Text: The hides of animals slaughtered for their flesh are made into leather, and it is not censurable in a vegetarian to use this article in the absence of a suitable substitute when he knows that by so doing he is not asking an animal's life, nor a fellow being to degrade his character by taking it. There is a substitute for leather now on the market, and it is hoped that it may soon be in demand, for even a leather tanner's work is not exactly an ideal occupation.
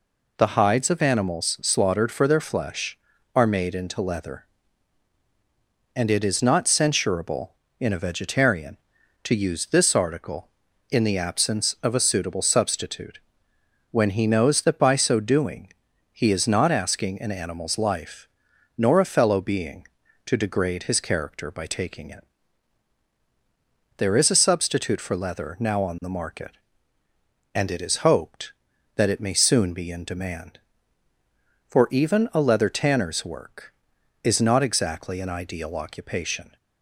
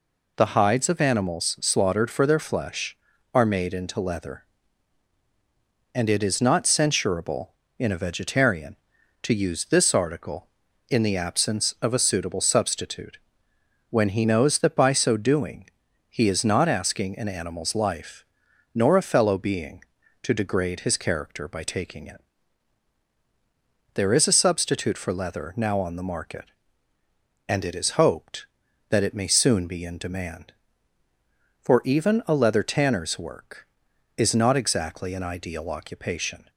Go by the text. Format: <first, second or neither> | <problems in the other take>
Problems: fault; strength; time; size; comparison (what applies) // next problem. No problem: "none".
neither | pauses between "substitute" and "when"; noticeable; the same in both // pauses between "doing" and "he"; the same in both